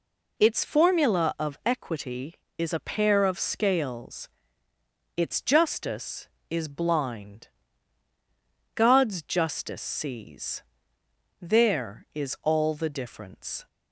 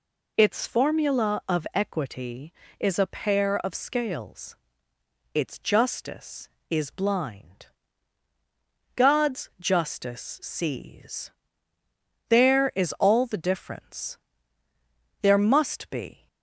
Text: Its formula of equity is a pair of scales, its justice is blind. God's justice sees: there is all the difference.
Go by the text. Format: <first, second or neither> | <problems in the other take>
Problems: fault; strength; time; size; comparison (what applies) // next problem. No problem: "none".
first | goes on to say "There must be"; noticeable; from 15.2 s on; 1.0 s long